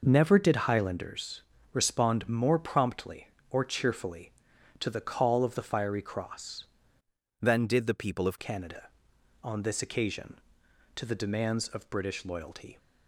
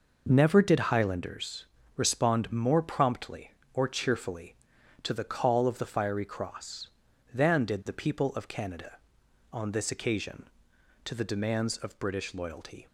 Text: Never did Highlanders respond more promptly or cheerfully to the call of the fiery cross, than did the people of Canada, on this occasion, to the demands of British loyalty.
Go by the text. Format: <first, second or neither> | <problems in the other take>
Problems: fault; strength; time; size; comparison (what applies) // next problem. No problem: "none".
second | pauses between "Highlanders" and "respond"; slight; at 1.4 s; 0.28 s long; slight in the second // changes voice from "than" to "of"; from 7.4 to 8.3 s; 0.9 s long